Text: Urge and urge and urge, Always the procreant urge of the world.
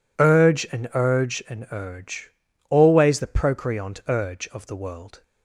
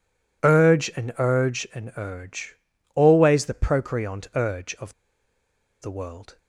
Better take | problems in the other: first | pauses between "of" and "the"; noticeable; at 4.9 s; 0.87 s long

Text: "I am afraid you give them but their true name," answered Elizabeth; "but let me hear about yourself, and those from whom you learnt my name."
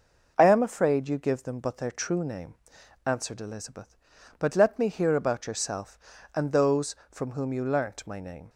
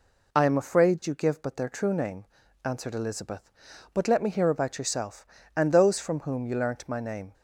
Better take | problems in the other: first | skips "them"; at 1.4 s

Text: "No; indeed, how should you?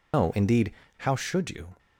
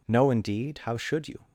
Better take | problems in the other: second | loses the start of "No"; at 0.1 s; 125 ms

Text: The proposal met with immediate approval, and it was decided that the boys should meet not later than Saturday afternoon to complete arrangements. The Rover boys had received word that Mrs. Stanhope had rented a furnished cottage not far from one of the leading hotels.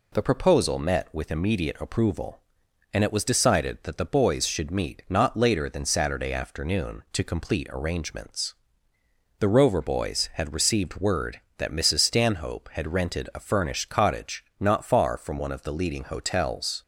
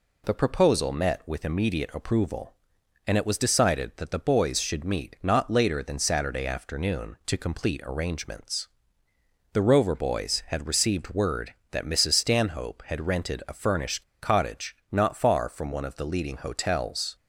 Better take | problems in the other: first | pauses between "furnished" and "cottage"; slight; at 14.0 s; 0.21 s long // pauses between "cottage" and "not"; slight; at 14.7 s; 0.16 s long; slight in the first

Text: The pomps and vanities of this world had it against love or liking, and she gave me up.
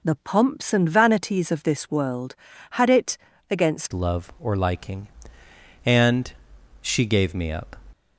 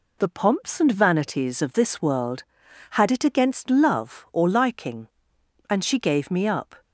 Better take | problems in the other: second | pauses between "it" and "against"; slight; at 3.1 s; 0.32 s long // changes voice at "love"; from 3.9 s on; 3.8 s long // pauses between "and" and "she"; noticeable; at 6.2 s; 0.52 s long

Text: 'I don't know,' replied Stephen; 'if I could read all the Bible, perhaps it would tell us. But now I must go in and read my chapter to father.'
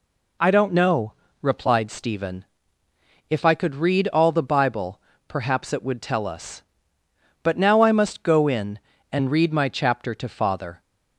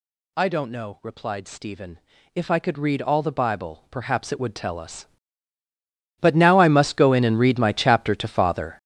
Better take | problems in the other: first | gets louder; strong; throughout; 11.5 dB

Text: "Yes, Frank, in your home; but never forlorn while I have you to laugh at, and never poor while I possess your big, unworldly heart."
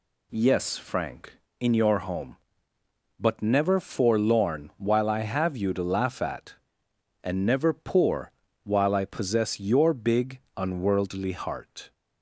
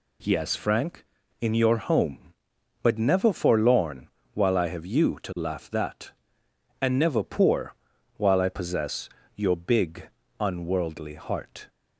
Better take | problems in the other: first | pauses between "forlorn" and "while"; slight; at 4.0 s; 0.28 s long // says "that" for "at"; at 5.6 s // pauses between "poor" and "while"; at 7.7 s; 0.42 s long; slight in the first // pauses between "possess" and "your"; slight; at 9.1 s; 0.26 s long

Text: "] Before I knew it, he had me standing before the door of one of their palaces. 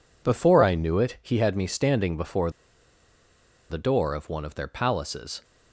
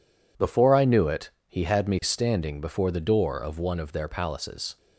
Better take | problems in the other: second | pauses between "before" and "the"; at 2.4 s; 1.2 s long

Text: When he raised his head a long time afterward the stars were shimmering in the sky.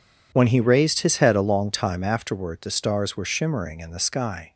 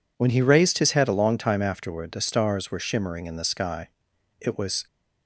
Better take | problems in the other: first | goes on to say "It was"; slight; from 4.4 s on; 0.46 s long

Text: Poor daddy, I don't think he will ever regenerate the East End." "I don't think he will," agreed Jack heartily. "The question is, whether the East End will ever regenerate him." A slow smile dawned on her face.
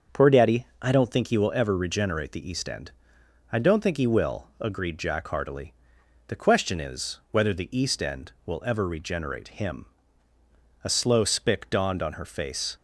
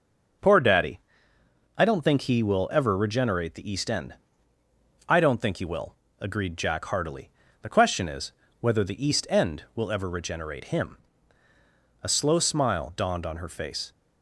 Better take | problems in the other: second | starts louder than the rest; until 1.2 s; 6.5 dB; also in the second // says "spick" for "smile"; at 11.2 s

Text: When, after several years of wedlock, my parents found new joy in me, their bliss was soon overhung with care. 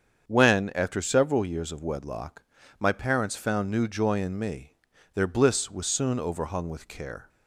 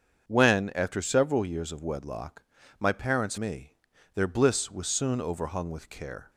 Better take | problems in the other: first | starts louder than the rest; until 1.2 s; 7 dB; strong in the first // skips "found new joy in"; at 3.3 s

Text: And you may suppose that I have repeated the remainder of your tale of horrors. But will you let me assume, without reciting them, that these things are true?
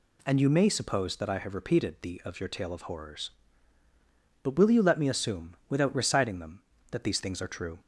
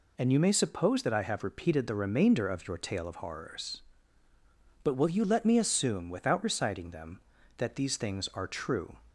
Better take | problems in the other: second | skips "remainder"; at 2.2 s

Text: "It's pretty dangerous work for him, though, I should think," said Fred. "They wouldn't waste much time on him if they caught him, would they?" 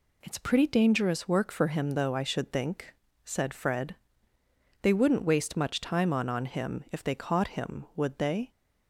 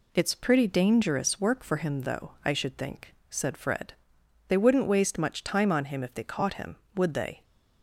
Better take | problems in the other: second | says "on" twice; at 6.2 s

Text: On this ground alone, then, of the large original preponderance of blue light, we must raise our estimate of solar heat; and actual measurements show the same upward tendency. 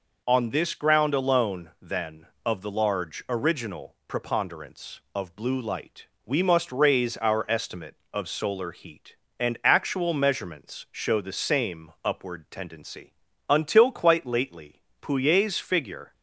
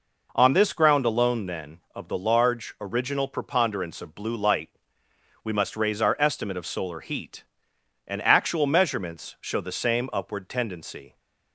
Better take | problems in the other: second | goes on to say "Until quite lately Pouillet's figure"; strong; from 13.4 s on; 2.6 s long

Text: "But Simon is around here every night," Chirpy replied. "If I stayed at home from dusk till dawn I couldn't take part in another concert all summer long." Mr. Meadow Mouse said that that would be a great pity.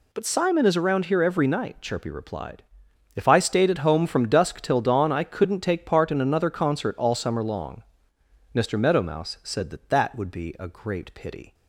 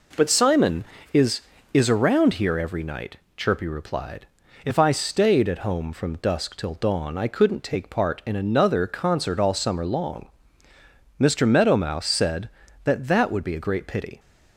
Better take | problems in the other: first | says "is" twice; at 1.7 s

